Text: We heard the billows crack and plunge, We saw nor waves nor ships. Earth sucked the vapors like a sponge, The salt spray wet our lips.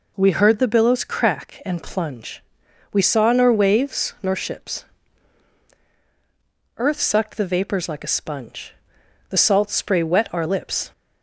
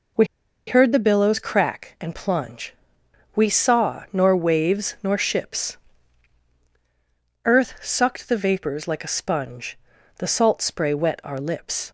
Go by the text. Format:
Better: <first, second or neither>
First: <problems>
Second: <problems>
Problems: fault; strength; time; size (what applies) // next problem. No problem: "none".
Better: first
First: none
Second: pauses between "We" and "heard"; at 0.2 s; 0.41 s long